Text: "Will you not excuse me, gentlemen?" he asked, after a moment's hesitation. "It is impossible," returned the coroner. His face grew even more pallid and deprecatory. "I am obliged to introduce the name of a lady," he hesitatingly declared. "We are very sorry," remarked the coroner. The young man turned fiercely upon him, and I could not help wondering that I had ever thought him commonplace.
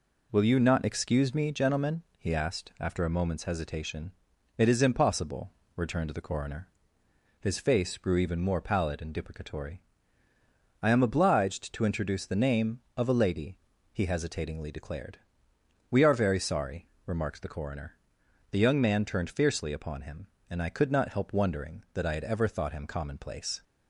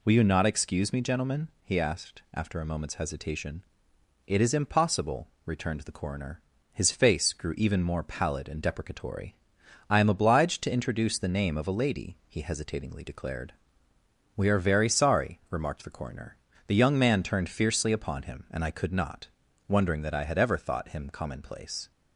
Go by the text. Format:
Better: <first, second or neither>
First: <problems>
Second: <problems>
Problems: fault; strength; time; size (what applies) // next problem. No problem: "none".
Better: first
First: none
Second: skips "help"; at 19.4 s